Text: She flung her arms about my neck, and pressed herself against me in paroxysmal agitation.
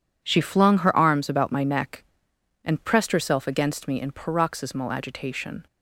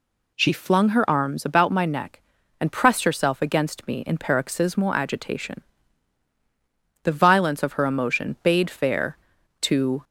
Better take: first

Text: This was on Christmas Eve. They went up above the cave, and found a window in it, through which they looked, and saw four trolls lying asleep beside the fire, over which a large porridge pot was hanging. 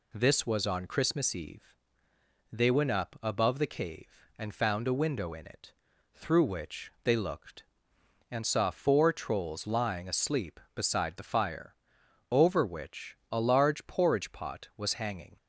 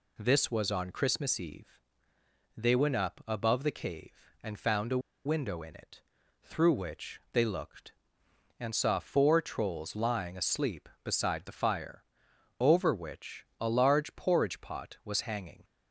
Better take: first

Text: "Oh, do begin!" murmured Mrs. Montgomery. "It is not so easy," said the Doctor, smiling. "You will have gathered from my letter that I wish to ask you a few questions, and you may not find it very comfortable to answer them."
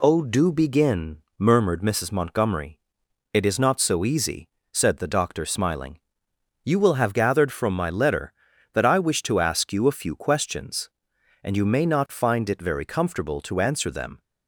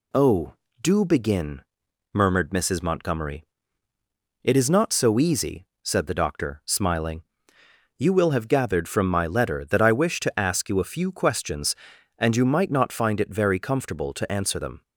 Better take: first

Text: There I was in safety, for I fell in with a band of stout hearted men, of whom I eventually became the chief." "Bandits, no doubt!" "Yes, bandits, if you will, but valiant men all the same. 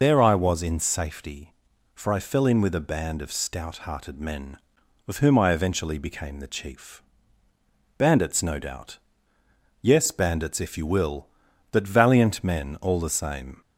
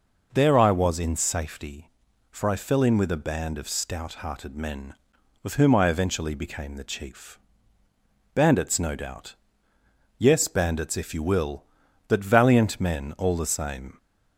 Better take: second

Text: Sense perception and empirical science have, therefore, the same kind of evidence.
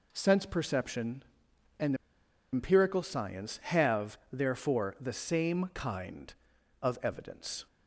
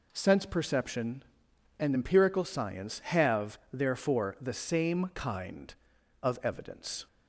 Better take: second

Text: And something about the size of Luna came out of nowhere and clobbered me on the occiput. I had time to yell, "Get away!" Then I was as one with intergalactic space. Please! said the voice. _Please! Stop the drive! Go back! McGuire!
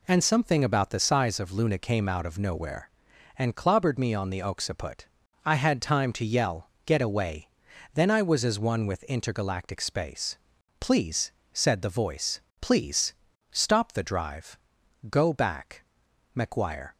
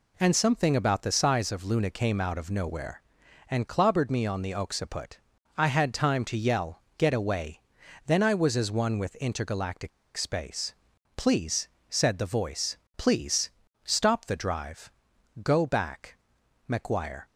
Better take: first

